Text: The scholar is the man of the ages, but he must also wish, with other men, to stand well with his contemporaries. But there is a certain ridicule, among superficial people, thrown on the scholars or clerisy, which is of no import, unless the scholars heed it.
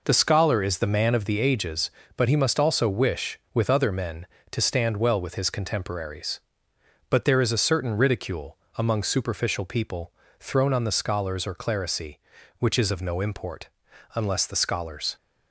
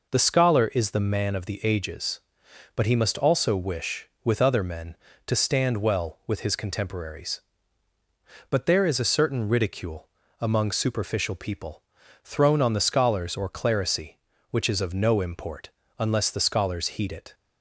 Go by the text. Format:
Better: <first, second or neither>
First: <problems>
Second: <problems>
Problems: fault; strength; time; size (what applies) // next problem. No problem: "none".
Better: second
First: stops before "heed it"; at 15.1 s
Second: none